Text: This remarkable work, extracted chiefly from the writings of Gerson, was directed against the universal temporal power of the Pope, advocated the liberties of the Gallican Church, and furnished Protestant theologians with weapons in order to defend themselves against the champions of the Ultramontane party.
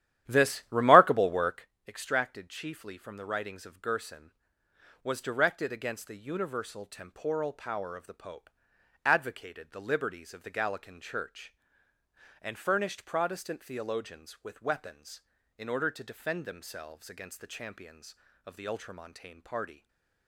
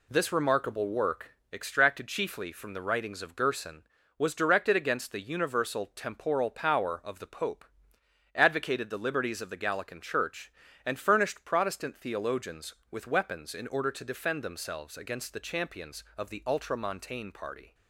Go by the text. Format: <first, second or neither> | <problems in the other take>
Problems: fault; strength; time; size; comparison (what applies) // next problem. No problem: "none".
second | starts louder than the rest; strong; until 1.7 s; 12 dB // stays silent after the last word; slight; from 19.7 s on; 0.5 s long